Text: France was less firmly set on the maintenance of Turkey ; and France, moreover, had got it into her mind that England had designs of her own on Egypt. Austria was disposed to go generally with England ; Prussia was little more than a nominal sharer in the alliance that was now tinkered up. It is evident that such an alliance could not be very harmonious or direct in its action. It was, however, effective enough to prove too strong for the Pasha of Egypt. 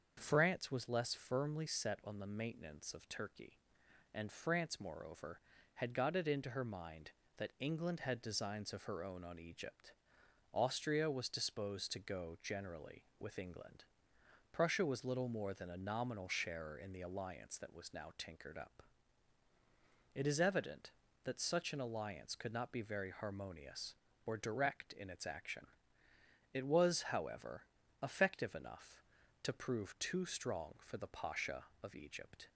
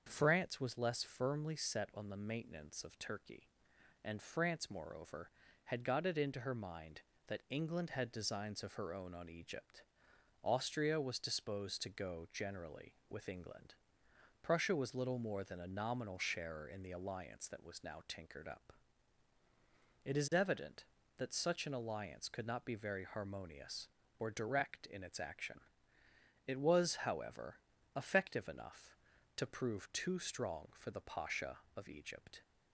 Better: neither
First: starts louder than the rest; until 1.2 s; 6.5 dB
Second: starts louder than the rest; until 1.1 s; 6.5 dB

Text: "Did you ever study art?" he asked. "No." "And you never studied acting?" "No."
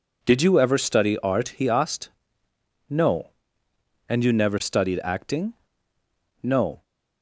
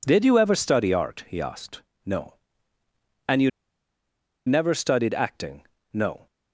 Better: first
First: none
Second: pauses between "you" and "never"; noticeable; at 3.4 s; 0.96 s long

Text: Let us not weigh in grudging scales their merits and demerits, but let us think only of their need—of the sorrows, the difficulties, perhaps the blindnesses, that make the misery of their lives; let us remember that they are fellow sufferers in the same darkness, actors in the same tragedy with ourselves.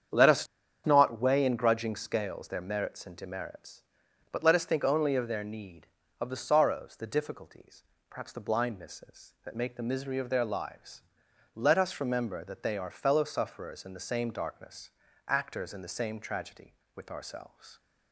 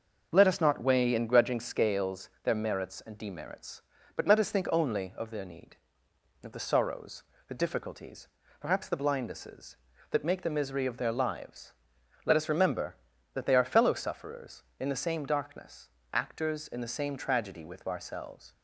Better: second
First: starts louder than the rest; strong; until 1.5 s; 8 dB // pauses between "us" and "not"; at 0.4 s; 0.38 s long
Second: none

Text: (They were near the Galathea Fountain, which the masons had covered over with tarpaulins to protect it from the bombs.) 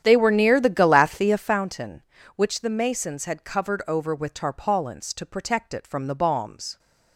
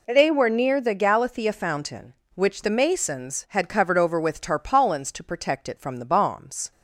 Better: second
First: starts louder than the rest; strong; until 1.6 s; 10 dB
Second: none

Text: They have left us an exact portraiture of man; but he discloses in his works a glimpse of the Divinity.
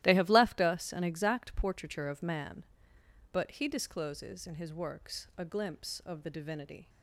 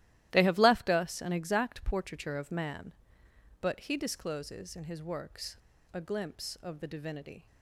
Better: first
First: starts louder than the rest; strong; until 1.0 s; 14.5 dB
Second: starts louder than the rest; strong; until 1.3 s; 14.5 dB // pauses between "works" and "a"; at 5.5 s; 0.36 s long

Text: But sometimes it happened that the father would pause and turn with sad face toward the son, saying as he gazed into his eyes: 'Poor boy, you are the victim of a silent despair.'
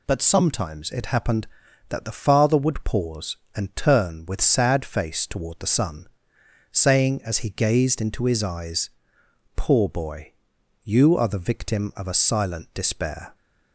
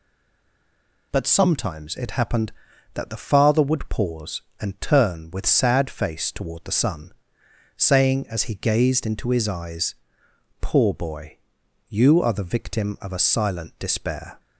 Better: first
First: none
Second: stays silent before the first word; until 1.1 s; 1.1 s long

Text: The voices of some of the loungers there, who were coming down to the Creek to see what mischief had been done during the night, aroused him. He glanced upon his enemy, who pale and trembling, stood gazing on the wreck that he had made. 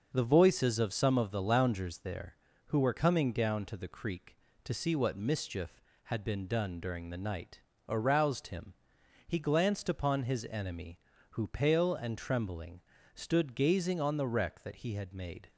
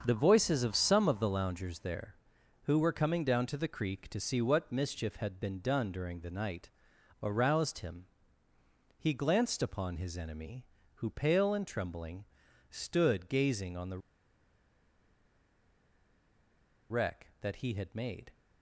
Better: first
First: starts louder than the rest; noticeable; until 1.1 s; 6 dB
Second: starts louder than the rest; until 1.0 s; 6.5 dB // pauses between "the" and "wreck"; strong; at 13.9 s; 2.9 s long

